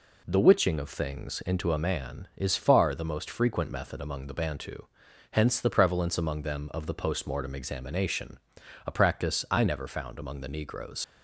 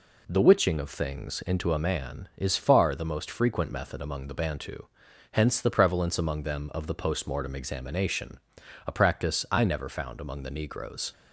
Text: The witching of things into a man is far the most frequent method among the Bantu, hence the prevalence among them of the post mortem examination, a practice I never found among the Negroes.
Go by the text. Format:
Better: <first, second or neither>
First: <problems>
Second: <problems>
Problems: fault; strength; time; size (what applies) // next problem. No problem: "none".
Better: second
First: leaves "Negroes" unfinished; at 11.0 s; 55 ms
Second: none